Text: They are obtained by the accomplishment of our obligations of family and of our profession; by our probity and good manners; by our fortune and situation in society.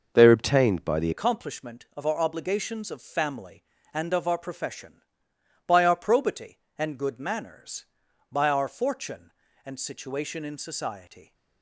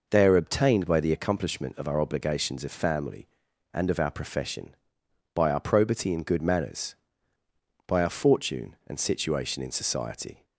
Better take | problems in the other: second | changes voice at "accomplishment"; from 1.1 s on; 10.2 s long

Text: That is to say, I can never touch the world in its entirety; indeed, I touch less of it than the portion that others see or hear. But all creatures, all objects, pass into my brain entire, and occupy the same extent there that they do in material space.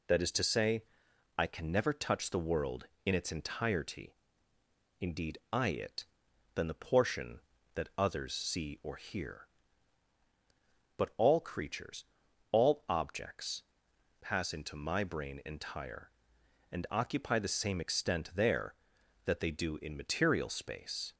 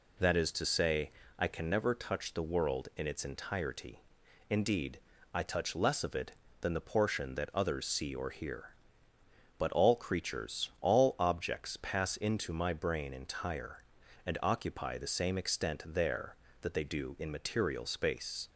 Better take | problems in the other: second | skips "touch less of"; at 5.6 s

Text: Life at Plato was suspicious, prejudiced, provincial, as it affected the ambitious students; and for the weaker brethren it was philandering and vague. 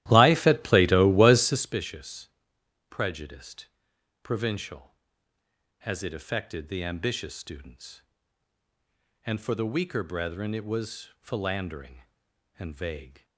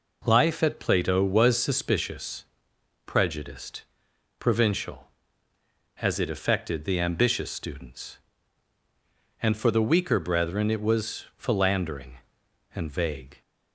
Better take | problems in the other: second | starts louder than the rest; strong; until 1.7 s; 14 dB

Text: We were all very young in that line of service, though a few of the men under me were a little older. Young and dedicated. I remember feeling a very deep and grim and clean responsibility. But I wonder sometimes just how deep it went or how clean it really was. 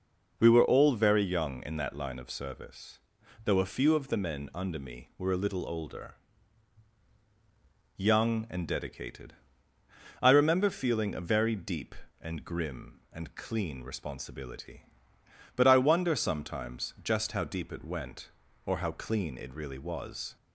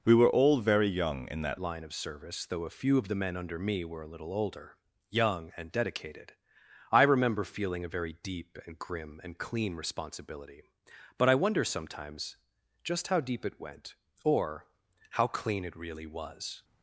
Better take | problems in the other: first | changes voice at "line"; from 1.5 s on; 15.1 s long // pauses between "sometimes" and "just"; noticeable; at 12.3 s; 0.48 s long // pauses between "or" and "how"; noticeable; at 14.6 s; 0.46 s long

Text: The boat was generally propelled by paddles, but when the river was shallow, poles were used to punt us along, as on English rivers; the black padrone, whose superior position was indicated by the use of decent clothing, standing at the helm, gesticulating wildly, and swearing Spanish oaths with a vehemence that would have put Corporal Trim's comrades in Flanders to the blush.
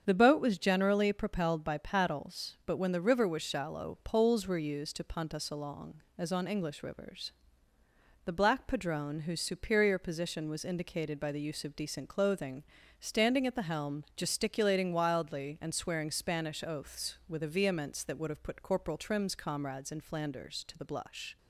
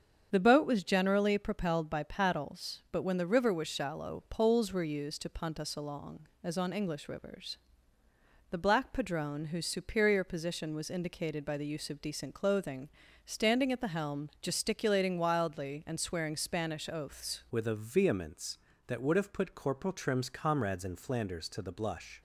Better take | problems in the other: first | starts louder than the rest; strong; until 1.3 s; 7.5 dB; strong in the first // changes voice at "with"; from 17.5 s on; 4.7 s long

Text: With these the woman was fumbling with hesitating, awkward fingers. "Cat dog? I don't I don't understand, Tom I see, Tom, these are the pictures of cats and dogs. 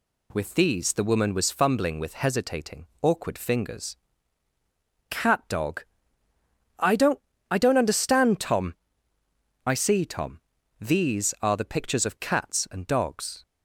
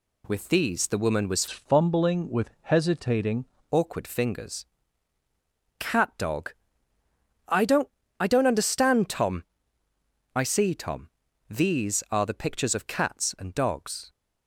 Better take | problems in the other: first | changes voice from "fumbling" to "hesitating"; from 1.5 to 3.4 s; 1.9 s long // pauses between "don't" and "I"; slight; at 7.8 s; 0.32 s long; slight in the first // pauses between "Tom" and "I"; noticeable; at 9.4 s; 0.90 s long; noticeable in the first

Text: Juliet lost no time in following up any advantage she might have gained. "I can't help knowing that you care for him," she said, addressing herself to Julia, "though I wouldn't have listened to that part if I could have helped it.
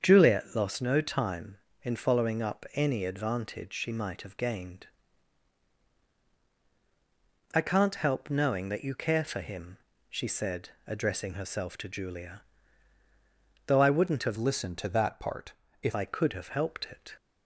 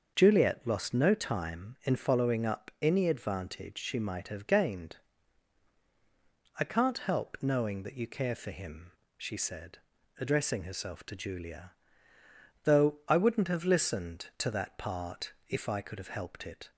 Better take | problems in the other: second | starts louder than the rest; strong; until 1.0 s; 7 dB; also in the second // changes voice from "listened" to "if"; from 14.3 to 15.9 s; 1.6 s long // pauses between "part" and "if"; slight; at 15.5 s; 0.28 s long; slight in the second

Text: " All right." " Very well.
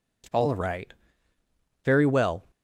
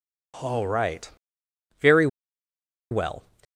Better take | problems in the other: first | pauses between "Very" and "well"; noticeable; at 2.0 s; 0.84 s long

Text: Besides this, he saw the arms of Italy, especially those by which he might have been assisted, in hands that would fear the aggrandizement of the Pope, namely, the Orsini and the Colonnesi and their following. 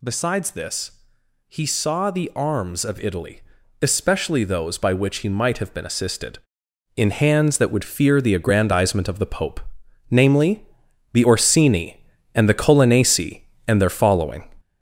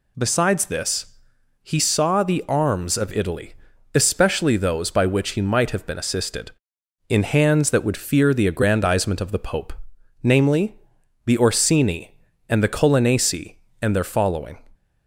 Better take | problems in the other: second | gets louder; noticeable; throughout; 6 dB

